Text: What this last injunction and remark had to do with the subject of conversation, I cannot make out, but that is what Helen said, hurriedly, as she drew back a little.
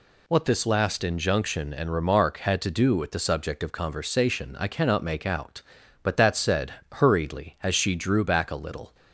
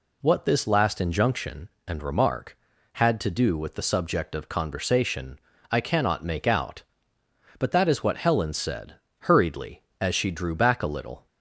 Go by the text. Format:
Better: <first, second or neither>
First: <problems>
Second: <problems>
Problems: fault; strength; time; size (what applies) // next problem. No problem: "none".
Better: second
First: skips "is what Helen"; at 6.3 s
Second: none